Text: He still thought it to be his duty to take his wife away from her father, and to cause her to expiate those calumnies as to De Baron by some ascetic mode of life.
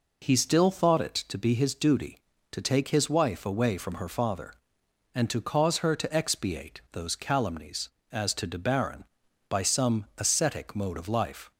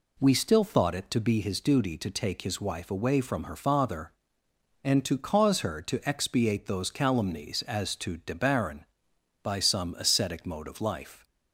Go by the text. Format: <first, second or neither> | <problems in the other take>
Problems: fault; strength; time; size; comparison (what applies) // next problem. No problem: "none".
first | says "We" for "He"; at 0.1 s